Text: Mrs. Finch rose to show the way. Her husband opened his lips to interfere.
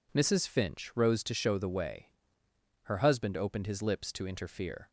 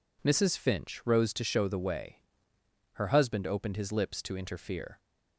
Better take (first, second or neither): neither